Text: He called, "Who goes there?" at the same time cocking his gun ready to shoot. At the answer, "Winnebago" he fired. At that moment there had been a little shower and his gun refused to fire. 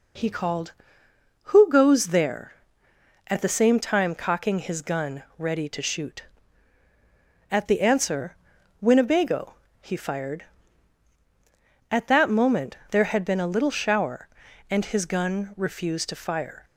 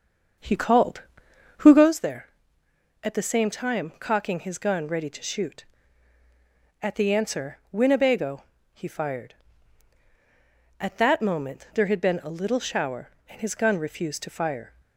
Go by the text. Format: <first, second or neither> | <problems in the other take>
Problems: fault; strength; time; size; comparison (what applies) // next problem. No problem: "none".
first | starts louder than the rest; until 1.9 s; 7 dB // pauses between "Winnebago" and "he"; slight; at 8.4 s; 0.30 s long; slight in the first